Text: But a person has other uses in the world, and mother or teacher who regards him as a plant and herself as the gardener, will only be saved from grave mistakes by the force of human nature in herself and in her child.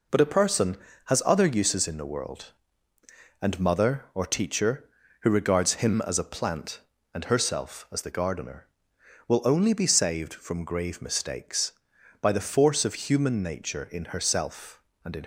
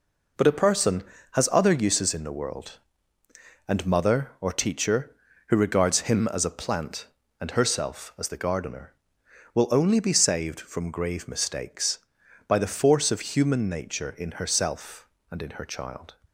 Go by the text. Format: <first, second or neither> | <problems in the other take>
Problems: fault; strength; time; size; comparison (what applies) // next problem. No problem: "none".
second | stops before "her child"; at 15.2 s